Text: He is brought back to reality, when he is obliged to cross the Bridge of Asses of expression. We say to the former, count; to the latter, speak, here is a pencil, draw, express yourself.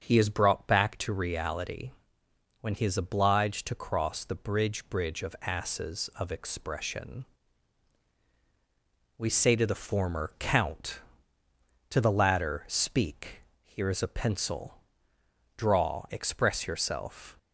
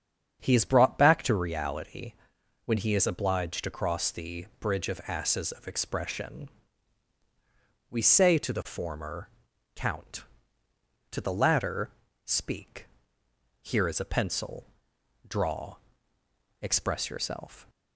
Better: second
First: starts louder than the rest; until 1.0 s; 7 dB // says "Bridge" twice; at 4.8 s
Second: starts louder than the rest; strong; until 1.4 s; 8 dB

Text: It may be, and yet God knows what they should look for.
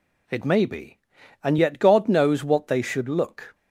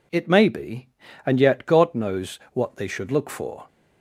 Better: second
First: stops before "for"; at 3.5 s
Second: none

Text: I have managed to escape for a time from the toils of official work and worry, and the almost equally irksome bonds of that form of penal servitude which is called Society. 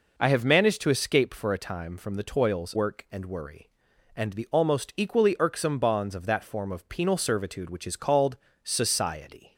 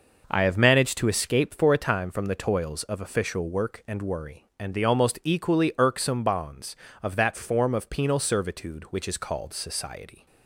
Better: second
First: skips "of official"; at 2.7 s // pauses between "called" and "Society"; slight; at 8.3 s; 0.26 s long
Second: none

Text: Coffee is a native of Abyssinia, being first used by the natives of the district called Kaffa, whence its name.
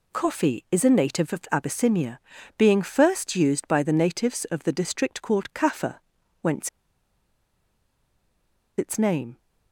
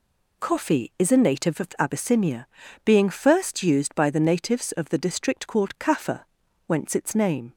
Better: second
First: pauses between "whence" and "its"; strong; at 6.6 s; 2.0 s long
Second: none

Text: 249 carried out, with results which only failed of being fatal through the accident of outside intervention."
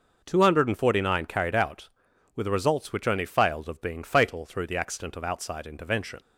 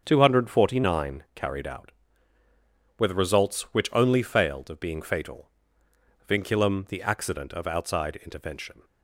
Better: first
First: none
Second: starts louder than the rest; strong; until 1.0 s; 7.5 dB // says "vinculum" for "through"; at 6.2 s

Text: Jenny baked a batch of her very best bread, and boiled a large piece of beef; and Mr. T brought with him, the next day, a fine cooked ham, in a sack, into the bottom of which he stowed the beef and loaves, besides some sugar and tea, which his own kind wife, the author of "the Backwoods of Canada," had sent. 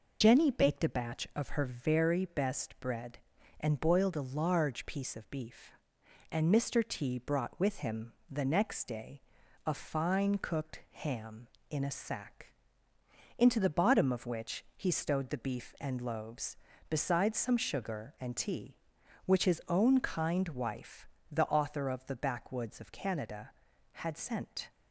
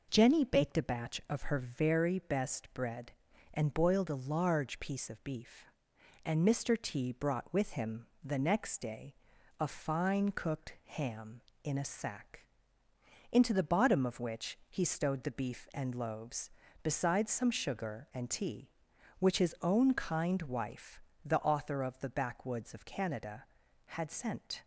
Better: second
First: loses the start of "Jenny"; at 0.2 s; 55 ms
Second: none

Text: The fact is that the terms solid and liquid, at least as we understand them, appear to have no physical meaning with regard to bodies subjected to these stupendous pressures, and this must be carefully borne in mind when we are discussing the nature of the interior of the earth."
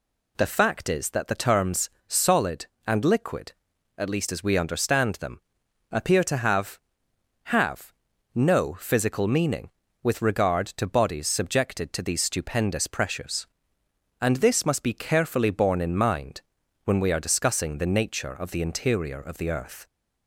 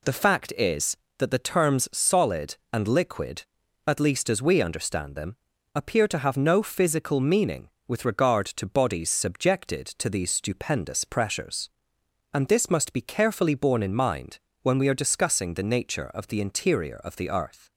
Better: second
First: pauses between "terms" and "solid"; slight; at 1.8 s; 0.20 s long // says "have" twice; at 7.4 s // pauses between "mind" and "when"; at 16.4 s; 0.42 s long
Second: pauses between "mind" and "when"; slight; at 14.3 s; 0.24 s long

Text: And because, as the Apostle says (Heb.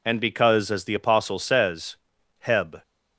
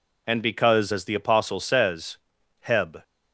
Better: neither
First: none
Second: none

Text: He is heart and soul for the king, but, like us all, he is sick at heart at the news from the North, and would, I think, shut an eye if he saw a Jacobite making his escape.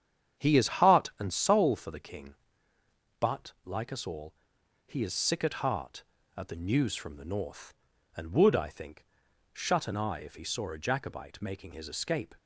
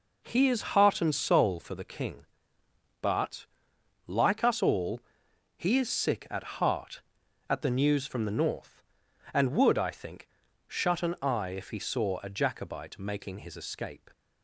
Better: second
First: starts louder than the rest; strong; until 1.7 s; 8.5 dB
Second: none

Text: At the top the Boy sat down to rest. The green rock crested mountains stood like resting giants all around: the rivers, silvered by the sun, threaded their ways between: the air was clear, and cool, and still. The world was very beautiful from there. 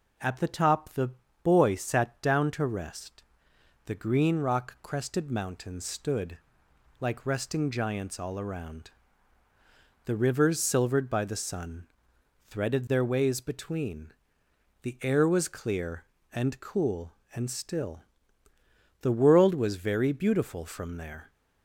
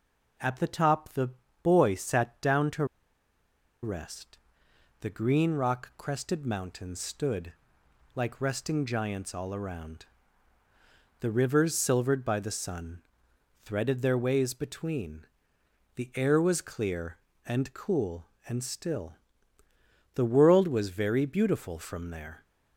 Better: first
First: pauses between "the" and "Boy"; slight; at 1.1 s; 0.32 s long // pauses between "stood" and "like"; noticeable; at 6.3 s; 0.60 s long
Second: pauses between "the" and "Boy"; slight; at 1.3 s; 0.32 s long // pauses between "to" and "rest"; noticeable; at 2.8 s; 0.97 s long // pauses between "stood" and "like"; noticeable; at 7.5 s; 0.60 s long

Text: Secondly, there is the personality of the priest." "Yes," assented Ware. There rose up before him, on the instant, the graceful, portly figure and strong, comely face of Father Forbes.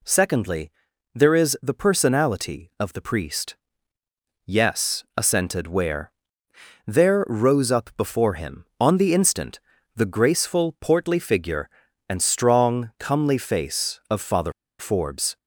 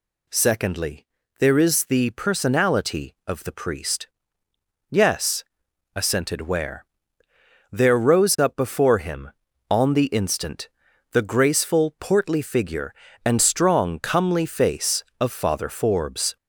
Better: second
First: pauses between "Father" and "Forbes"; slight; at 14.5 s; 0.27 s long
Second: none

